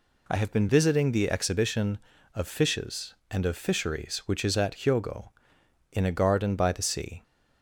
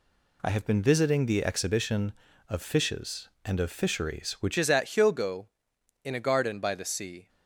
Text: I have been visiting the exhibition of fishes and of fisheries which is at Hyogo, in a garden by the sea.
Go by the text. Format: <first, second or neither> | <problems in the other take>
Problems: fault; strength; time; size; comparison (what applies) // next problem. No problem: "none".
first | changes voice at "is"; from 4.5 s on; 2.7 s long